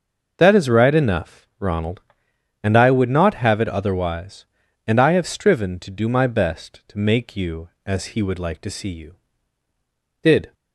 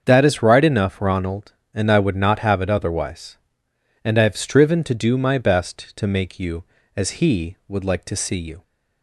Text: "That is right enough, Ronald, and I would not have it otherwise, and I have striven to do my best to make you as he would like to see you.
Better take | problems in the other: second | starts louder than the rest; until 1.3 s; 6.5 dB; also in the second // goes on to say "Did"; slight; from 10.2 s on; 0.32 s long

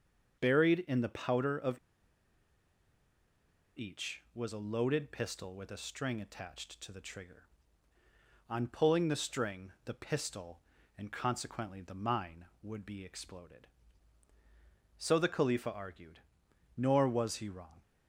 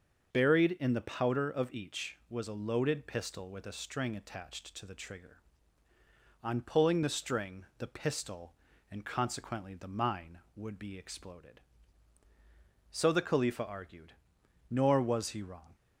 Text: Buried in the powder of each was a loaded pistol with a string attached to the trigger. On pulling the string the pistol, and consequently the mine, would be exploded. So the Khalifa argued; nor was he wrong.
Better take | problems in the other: second | starts louder than the rest; until 1.4 s; 6.5 dB; also in the second // pauses between "of" and "each"; strong; at 1.7 s; 2.0 s long

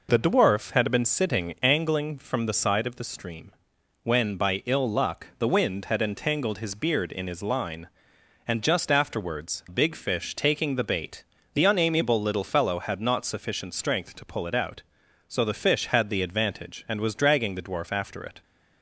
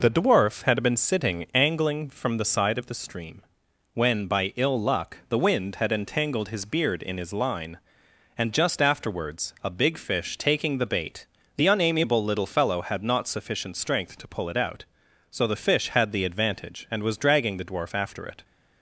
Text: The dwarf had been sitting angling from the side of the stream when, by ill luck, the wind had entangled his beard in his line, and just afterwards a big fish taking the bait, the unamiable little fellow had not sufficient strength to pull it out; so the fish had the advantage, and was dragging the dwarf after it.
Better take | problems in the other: second | pauses between "stream" and "when"; noticeable; at 3.5 s; 0.50 s long; noticeable in the second // skips "a"; at 9.6 s

